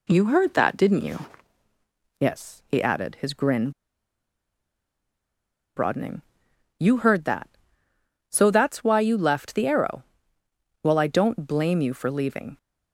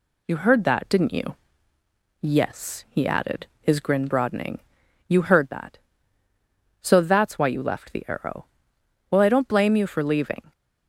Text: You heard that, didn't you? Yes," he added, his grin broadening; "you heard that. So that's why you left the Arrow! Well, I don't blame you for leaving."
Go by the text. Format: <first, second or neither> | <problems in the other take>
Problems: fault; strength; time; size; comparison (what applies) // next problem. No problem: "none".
second | pauses between "grin" and "broadening"; strong; at 3.6 s; 2.0 s long